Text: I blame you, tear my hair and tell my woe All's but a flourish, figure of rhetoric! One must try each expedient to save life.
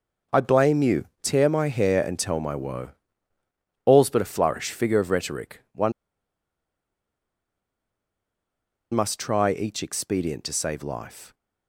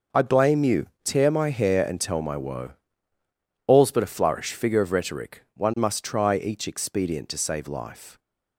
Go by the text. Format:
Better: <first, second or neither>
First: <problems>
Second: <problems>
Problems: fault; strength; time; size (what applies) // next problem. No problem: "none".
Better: second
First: pauses between "woe" and "All's"; noticeable; at 2.9 s; 0.96 s long // pauses between "One" and "must"; strong; at 5.9 s; 3.0 s long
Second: pauses between "woe" and "All's"; noticeable; at 2.7 s; 0.96 s long